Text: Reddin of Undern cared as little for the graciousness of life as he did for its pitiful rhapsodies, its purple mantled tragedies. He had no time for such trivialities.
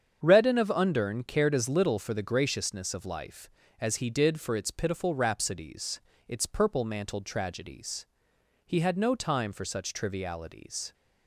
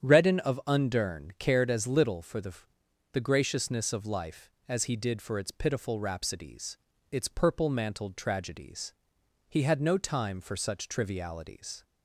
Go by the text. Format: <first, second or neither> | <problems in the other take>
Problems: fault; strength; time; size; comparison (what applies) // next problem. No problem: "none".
first | starts louder than the rest; strong; until 1.0 s; 9 dB; strong in the first // says "the" twice; at 3.1 s